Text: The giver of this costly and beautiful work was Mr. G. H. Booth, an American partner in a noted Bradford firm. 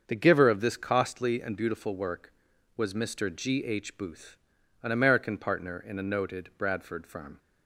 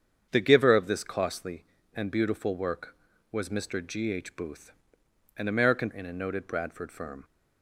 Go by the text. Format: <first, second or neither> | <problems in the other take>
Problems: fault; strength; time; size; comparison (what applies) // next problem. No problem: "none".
first | starts louder than the rest; strong; until 1.3 s; 7.5 dB; also in the first // skips "partner"; at 5.8 s